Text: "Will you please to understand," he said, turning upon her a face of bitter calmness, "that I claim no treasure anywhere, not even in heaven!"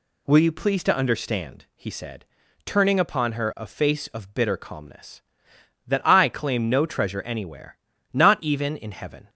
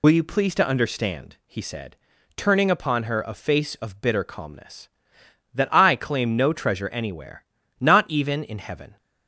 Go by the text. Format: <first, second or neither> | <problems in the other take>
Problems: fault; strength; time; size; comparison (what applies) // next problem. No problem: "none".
first | loses the start of "Will"; at 0.0 s; 65 ms